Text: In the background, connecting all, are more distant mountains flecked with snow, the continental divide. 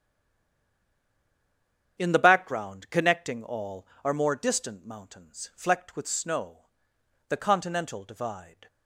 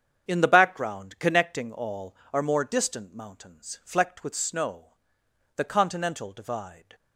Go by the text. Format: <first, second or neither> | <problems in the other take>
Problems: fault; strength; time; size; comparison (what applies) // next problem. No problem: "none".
second | stays silent before the first word; noticeable; until 1.9 s; 1.9 s long // starts louder than the rest; strong; until 3.0 s; 8 dB; strong in the second